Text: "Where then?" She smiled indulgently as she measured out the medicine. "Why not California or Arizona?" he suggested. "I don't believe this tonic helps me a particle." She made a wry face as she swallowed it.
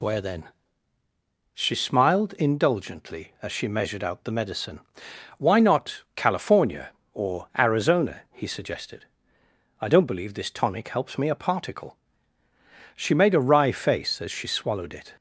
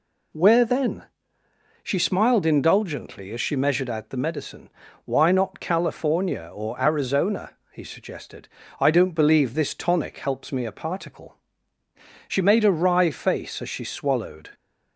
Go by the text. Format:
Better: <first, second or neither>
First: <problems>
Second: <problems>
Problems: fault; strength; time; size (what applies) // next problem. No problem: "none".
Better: first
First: none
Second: stops before "it"; at 14.5 s